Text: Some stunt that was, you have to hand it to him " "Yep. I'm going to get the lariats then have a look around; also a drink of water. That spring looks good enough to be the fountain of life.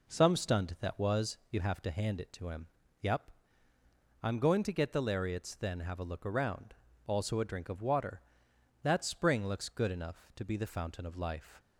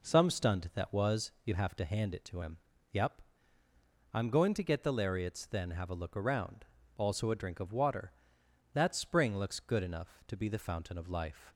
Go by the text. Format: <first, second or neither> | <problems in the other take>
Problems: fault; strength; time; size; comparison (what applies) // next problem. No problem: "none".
neither | none